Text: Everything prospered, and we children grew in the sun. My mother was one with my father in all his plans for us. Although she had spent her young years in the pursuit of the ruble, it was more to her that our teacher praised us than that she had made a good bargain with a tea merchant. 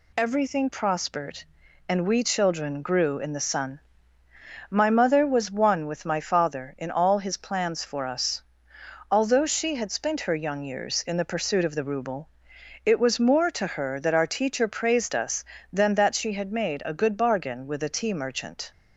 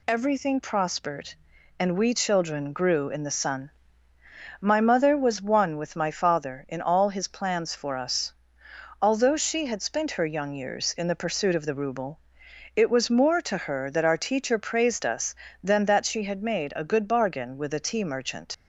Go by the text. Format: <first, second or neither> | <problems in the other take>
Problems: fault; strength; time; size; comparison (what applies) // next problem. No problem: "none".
first | leaves "merchant" unfinished; at 18.5 s; 65 ms